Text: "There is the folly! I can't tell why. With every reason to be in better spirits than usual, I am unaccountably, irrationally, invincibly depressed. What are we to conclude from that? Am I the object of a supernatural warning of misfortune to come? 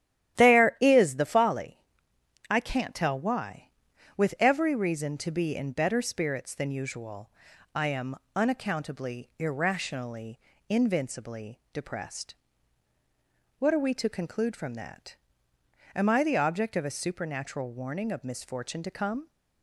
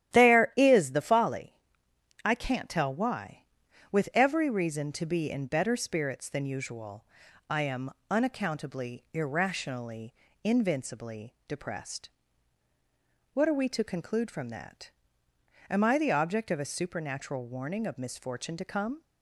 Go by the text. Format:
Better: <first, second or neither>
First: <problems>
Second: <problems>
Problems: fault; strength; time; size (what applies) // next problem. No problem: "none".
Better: neither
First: starts louder than the rest; strong; until 1.4 s; 12 dB // pauses between "am" and "unaccountably"; slight; at 8.1 s; 0.20 s long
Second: starts louder than the rest; strong; until 1.1 s; 11.5 dB // pauses between "am" and "unaccountably"; slight; at 7.9 s; 0.20 s long